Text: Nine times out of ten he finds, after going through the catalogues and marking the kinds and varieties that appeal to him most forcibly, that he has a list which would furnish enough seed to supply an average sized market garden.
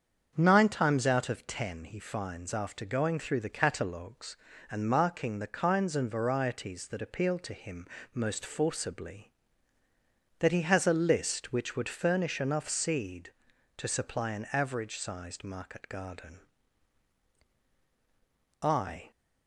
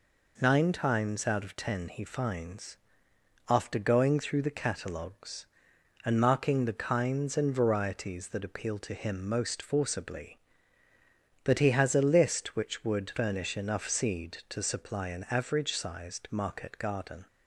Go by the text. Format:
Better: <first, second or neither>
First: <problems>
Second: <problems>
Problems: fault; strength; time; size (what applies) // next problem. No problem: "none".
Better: second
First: starts louder than the rest; strong; until 1.3 s; 7 dB // pauses between "him" and "most"; slight; at 7.8 s; 0.28 s long // goes on to say "I"; slight; from 18.6 s on; 0.48 s long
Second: none